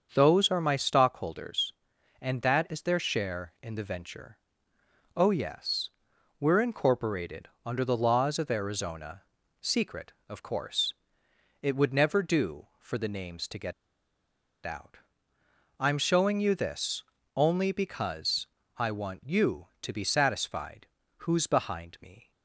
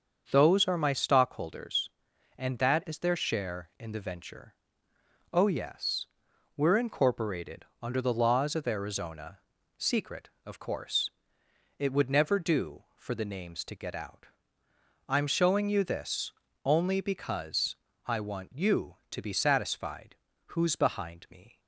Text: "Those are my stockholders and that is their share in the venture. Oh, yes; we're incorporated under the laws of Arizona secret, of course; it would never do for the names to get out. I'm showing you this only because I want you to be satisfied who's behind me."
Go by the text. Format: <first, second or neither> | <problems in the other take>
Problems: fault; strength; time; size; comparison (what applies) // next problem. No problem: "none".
second | starts louder than the rest; until 1.1 s; 7 dB; also in the second // pauses between "incorporated" and "under"; slight; at 7.4 s; 0.16 s long; slight in the second // pauses between "Arizona" and "secret"; at 9.2 s; 0.40 s long; also in the second // pauses between "get" and "out"; noticeable; at 13.7 s; 0.93 s long // pauses between "this" and "only"; slight; at 17.0 s; 0.32 s long; slight in the second // pauses between "because" and "I"; slight; at 18.4 s; 0.30 s long; slight in the second // pauses between "satisfied" and "who's"; slight; at 20.8 s; 0.34 s long; slight in the second